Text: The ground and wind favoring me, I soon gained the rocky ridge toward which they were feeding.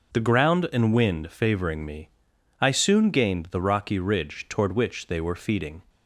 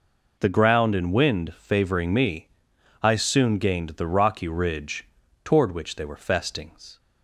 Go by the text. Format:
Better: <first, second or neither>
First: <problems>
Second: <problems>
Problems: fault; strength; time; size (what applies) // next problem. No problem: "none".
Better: first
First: none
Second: pauses between "ridge" and "toward"; at 5.0 s; 0.38 s long // says "festings" for "feeding"; at 6.1 s